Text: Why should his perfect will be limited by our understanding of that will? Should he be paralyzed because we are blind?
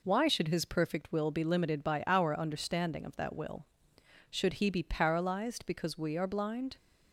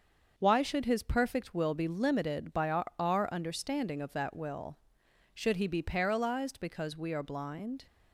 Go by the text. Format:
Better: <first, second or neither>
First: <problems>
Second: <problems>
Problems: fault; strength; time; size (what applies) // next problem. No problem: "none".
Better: first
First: none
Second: starts louder than the rest; until 1.3 s; 6.5 dB // says "our" twice; at 2.9 s